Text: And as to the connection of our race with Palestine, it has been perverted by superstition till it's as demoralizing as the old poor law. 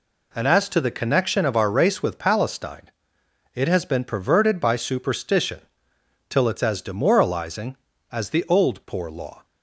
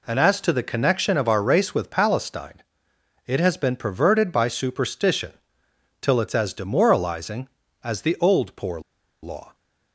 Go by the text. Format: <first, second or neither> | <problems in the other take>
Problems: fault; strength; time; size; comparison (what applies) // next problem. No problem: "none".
first | pauses between "superstition" and "till"; noticeable; at 5.3 s; 0.70 s long; noticeable in the first // pauses between "poor" and "law"; at 8.7 s; 0.42 s long